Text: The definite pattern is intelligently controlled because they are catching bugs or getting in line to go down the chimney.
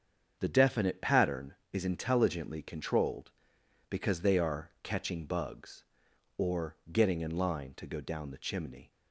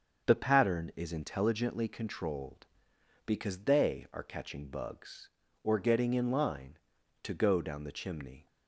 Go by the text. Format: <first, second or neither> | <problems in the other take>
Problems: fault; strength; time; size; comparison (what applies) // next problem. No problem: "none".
first | starts louder than the rest; until 1.3 s; 6.5 dB; strong in the first // skips "definite"; at 0.4 s